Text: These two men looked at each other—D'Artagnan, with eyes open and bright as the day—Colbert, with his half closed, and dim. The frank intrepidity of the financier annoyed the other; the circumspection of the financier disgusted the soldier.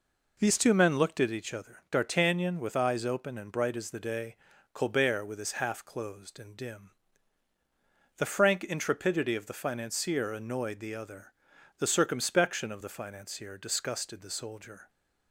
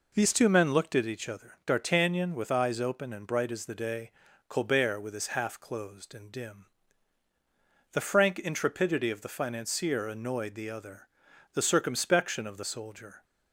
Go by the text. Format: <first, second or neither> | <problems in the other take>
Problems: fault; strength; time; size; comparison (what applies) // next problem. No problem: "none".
first | skips "financier disgusted the"; at 12.6 s